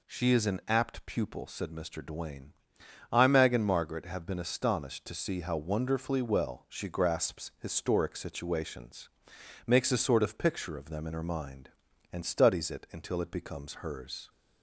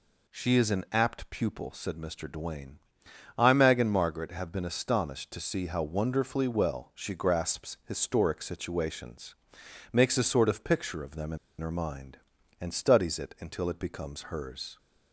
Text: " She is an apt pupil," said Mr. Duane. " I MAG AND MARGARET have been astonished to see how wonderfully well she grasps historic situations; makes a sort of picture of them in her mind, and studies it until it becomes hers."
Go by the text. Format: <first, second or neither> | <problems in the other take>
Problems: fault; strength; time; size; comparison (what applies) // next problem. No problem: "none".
first | pauses between "in" and "her"; slight; at 11.3 s; 0.21 s long